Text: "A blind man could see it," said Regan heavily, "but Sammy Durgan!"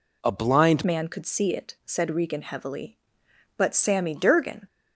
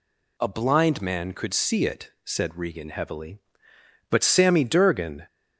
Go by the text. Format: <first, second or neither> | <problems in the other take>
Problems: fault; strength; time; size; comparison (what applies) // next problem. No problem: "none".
second | changes voice at "man"; from 0.8 s on; 3.8 s long